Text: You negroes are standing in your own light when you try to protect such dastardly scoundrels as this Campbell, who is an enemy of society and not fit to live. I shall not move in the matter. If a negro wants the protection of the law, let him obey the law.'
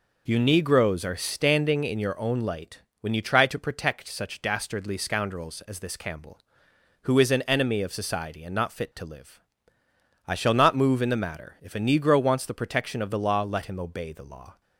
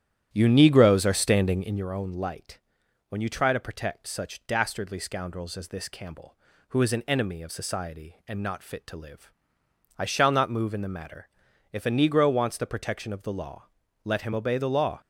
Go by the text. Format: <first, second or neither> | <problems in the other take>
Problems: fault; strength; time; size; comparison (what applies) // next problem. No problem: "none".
first | starts louder than the rest; strong; until 1.9 s; 11 dB // pauses between "light" and "when"; noticeable; at 2.5 s; 0.50 s long; slight in the first